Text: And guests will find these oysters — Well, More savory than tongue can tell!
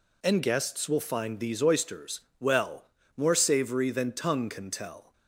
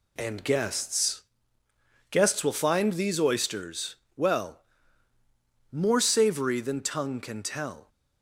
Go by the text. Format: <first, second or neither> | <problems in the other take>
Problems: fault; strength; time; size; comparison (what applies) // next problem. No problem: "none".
first | says "guests" twice; at 2.0 s